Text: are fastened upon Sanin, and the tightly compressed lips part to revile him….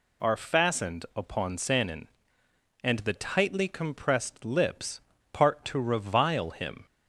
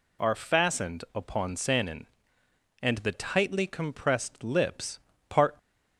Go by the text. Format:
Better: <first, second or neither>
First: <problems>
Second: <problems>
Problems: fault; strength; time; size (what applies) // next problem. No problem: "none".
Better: first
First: pauses between "lips" and "part"; slight; at 5.0 s; 0.32 s long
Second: pauses between "lips" and "part"; slight; at 4.9 s; 0.30 s long // stops before "to revile him"; at 5.5 s